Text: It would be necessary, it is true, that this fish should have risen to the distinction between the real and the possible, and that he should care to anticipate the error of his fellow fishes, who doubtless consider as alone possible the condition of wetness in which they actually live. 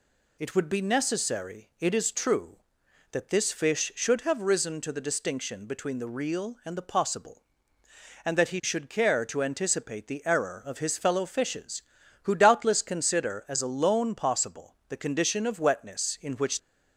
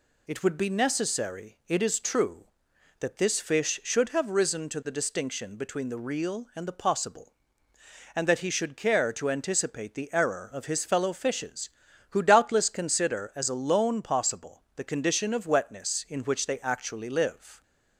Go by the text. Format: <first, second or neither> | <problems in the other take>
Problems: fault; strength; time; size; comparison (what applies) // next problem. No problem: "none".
second | stops before "they actually live"; at 16.5 s